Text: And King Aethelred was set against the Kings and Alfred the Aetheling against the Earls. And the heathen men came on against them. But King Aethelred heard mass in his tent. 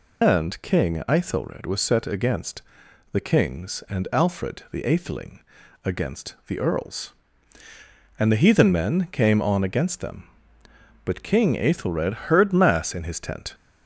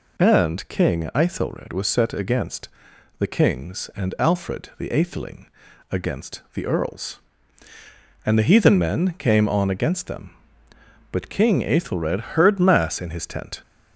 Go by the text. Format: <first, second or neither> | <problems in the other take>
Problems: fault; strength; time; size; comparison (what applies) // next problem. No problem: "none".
second | loses the start of "And"; at 0.2 s; 90 ms // pauses between "against" and "the"; noticeable; at 2.6 s; 0.50 s long; noticeable in the second // pauses between "Aetheling" and "against"; at 5.4 s; 0.44 s long; also in the second